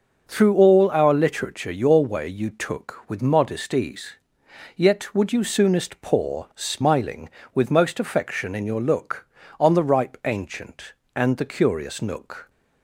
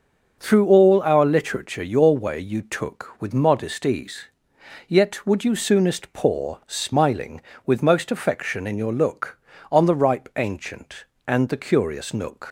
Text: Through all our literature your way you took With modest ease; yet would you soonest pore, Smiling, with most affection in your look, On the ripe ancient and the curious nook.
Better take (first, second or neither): first